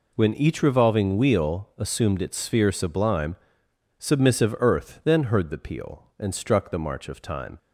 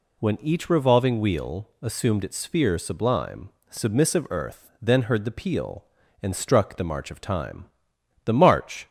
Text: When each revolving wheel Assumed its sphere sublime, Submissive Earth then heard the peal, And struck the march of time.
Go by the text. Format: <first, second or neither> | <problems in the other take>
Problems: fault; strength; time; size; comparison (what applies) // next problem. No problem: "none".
first | goes on to say "The march"; noticeable; from 8.2 s on; 0.64 s long